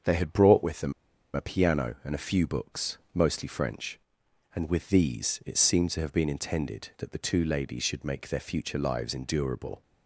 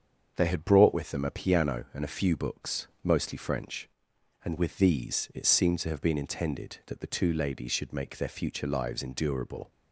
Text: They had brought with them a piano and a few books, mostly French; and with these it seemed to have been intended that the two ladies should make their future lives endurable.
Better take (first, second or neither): second